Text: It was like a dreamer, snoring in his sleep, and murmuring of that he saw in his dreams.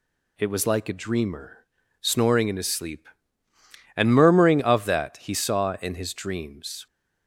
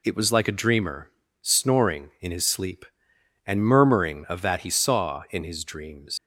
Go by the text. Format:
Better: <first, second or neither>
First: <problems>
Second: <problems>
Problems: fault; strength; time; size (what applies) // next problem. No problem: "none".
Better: first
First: none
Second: leaves "dreams" unfinished; at 6.1 s; 130 ms